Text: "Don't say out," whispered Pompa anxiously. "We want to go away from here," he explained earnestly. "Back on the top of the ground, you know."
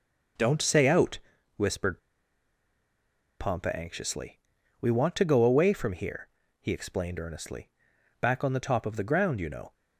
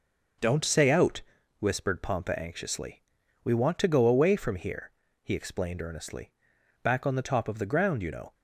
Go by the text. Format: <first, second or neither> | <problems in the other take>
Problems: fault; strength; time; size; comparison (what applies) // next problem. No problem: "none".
second | pauses between "whispered" and "Pompa"; strong; at 1.9 s; 1.4 s long